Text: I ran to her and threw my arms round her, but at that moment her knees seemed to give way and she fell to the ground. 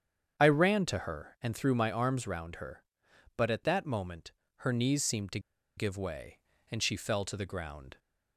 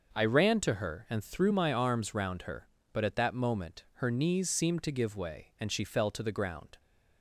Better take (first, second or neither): second